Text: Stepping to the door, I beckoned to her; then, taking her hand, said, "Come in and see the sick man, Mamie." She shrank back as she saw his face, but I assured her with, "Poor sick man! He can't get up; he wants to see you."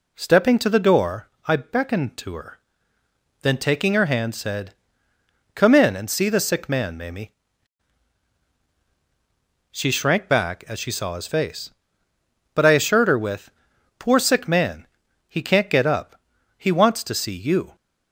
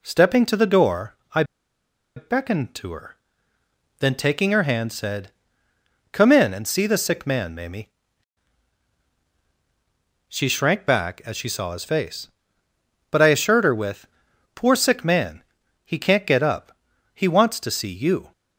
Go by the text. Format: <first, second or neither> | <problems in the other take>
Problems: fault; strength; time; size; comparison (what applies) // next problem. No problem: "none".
first | pauses between "I" and "beckoned"; noticeable; at 1.4 s; 0.73 s long